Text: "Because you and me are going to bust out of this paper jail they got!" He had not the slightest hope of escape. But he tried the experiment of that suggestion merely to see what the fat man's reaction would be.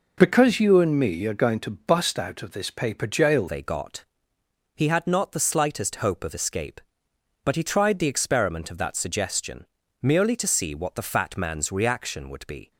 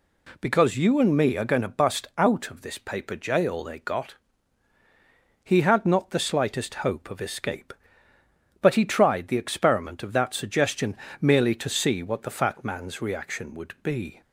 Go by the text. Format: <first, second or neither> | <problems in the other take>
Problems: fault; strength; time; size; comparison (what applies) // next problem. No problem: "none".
second | changes voice at "they"; from 3.4 s on; 9.3 s long // pauses between "suggestion" and "merely"; slight; at 9.6 s; 0.36 s long; slight in the second